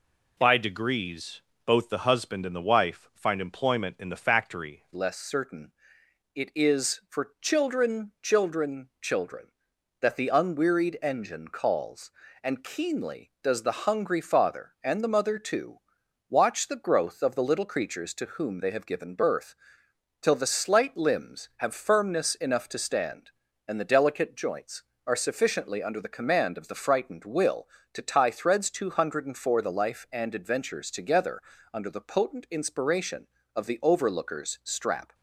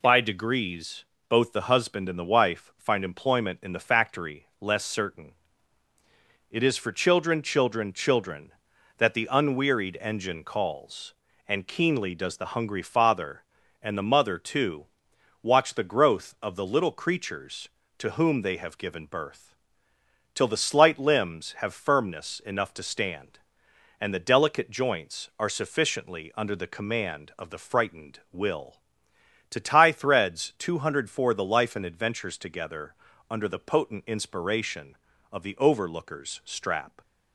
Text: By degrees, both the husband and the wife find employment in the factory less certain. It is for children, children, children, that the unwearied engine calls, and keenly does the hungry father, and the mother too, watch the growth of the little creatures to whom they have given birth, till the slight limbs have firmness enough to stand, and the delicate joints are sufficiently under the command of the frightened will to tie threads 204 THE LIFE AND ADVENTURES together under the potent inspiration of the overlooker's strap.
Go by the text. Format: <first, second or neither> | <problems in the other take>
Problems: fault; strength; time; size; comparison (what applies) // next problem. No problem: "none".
second | changes voice at "less"; from 4.9 s on; 30.2 s long // pauses between "together" and "under"; slight; at 31.3 s; 0.34 s long; slight in the second